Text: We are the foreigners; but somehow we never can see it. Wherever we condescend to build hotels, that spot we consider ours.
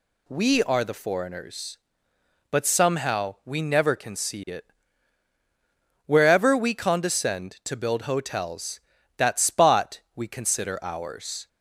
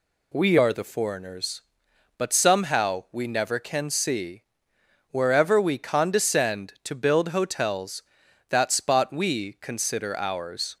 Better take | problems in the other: first | skips "it"; at 4.7 s

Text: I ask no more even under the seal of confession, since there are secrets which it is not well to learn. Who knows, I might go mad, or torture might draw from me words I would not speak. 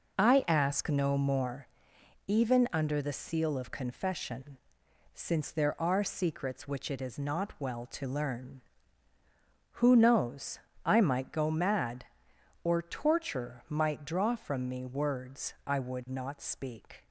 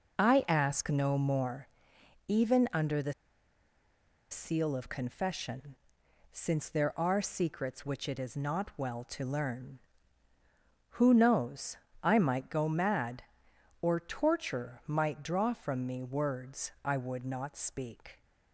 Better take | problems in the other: first | pauses between "more" and "even"; noticeable; at 1.6 s; 0.60 s long; noticeable in the first // pauses between "the" and "seal"; at 3.1 s; 1.1 s long

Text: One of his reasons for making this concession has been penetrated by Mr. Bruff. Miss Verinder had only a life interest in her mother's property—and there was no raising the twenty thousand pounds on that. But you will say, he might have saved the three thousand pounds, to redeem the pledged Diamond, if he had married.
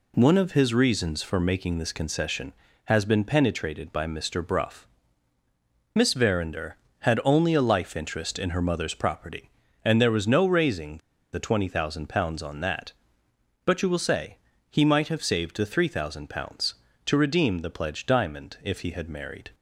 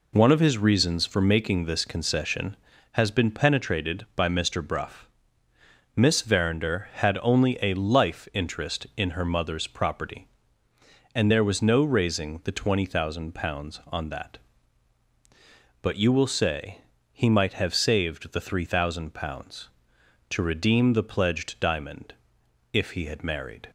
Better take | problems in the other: second | pauses between "raising" and "the"; slight; at 10.9 s; 0.34 s long

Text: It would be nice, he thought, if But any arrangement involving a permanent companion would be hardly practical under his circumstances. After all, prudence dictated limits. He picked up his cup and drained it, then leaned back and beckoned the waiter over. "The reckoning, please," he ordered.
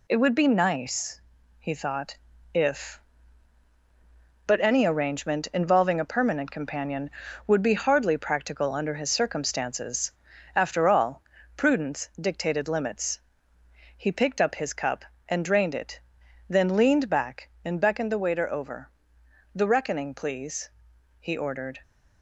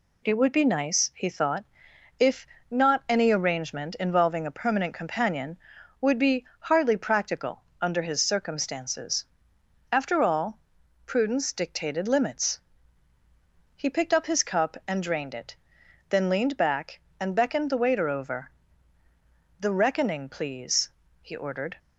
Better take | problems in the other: first | says "Not" for "But"; at 2.7 s // pauses between "practical" and "under"; slight; at 7.6 s; 0.16 s long

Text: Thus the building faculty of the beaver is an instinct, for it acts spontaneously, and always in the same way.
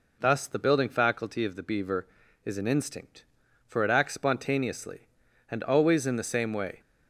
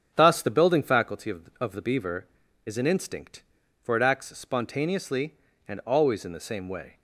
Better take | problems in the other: first | starts louder than the rest; strong; until 1.1 s; 7.5 dB // says "of" twice; at 1.6 s

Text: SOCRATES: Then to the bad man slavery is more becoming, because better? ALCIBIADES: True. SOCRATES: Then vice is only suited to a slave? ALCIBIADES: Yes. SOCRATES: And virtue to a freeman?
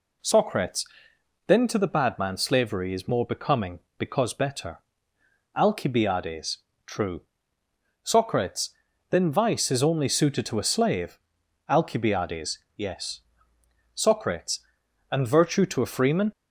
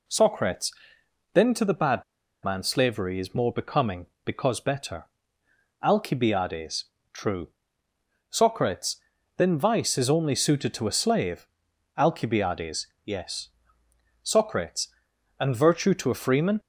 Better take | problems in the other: first | pauses between "bad" and "man"; at 2.0 s; 0.40 s long

